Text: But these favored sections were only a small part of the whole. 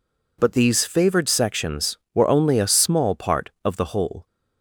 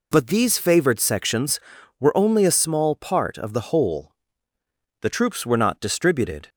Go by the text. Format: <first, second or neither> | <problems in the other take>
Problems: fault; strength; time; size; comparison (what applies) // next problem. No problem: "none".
first | goes on to say "The troops were not distributed"; from 5.0 s on; 1.4 s long